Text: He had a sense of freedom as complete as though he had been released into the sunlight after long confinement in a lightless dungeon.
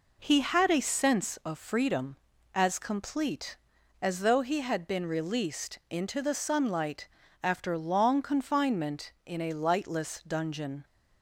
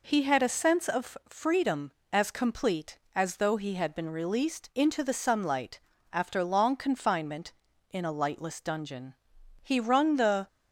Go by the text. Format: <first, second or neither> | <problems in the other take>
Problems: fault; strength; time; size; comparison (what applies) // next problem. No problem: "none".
first | pauses between "sunlight" and "after"; slight; at 5.8 s; 0.32 s long; slight in the first // goes on to say "He wrung the"; noticeable; from 9.6 s on; 0.84 s long